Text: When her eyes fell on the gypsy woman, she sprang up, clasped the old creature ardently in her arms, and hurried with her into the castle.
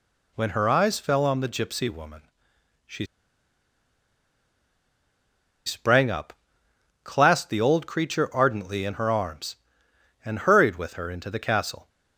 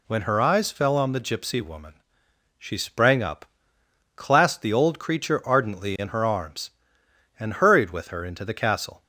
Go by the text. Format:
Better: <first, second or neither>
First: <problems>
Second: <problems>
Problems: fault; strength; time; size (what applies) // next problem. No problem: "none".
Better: second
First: pauses between "she" and "sprang"; strong; at 3.0 s; 2.6 s long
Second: none